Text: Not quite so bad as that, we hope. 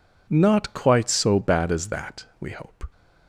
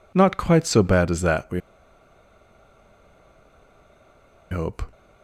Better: first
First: none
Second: pauses between "we" and "hope"; strong; at 1.6 s; 2.9 s long

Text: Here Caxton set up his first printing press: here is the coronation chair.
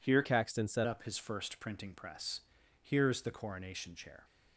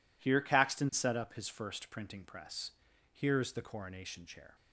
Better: second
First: changes voice from "Caxton" to "set"; from 0.2 to 0.8 s; 0.6 s long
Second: none

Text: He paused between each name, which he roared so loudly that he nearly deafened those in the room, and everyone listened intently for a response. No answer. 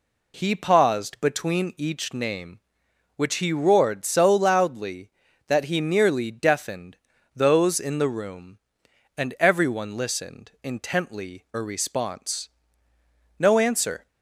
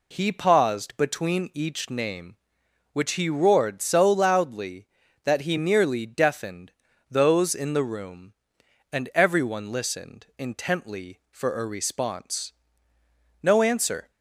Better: second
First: pauses between "deafened" and "those"; slight; at 6.9 s; 0.36 s long // skips "for"; at 11.5 s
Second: pauses between "deafened" and "those"; slight; at 6.7 s; 0.36 s long

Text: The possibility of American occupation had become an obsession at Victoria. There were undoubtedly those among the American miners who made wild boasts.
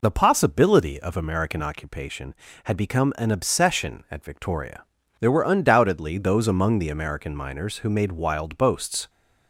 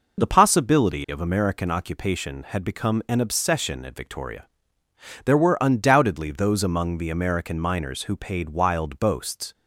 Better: first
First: none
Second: says "paid" for "made"; at 8.1 s

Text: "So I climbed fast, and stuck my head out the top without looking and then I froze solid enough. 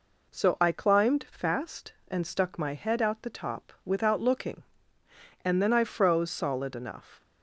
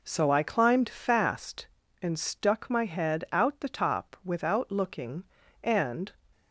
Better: first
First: none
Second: stops before "then I froze solid enough"; at 6.3 s

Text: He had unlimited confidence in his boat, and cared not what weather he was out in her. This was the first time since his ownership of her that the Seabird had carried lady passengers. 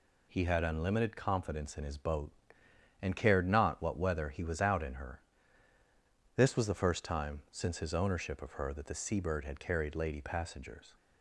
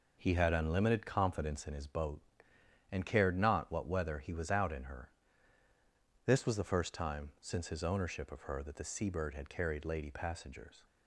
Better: first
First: none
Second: starts louder than the rest; noticeable; until 1.7 s; 4.5 dB

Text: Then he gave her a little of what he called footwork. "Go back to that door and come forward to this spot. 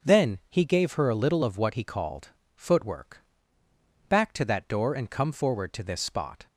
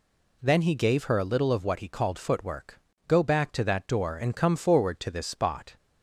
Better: second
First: starts louder than the rest; until 1.1 s; 6.5 dB // pauses between "called" and "footwork"; slight; at 2.2 s; 0.28 s long // skips "Go"; at 3.6 s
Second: none

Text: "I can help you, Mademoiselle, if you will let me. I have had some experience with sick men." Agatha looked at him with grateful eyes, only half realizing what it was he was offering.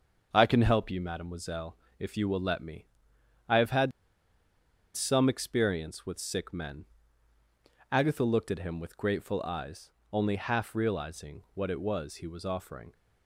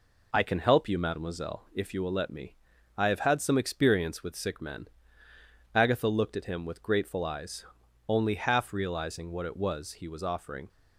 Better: second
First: starts louder than the rest; until 1.3 s; 6.5 dB // pauses between "had" and "some"; at 3.9 s; 1.0 s long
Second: none

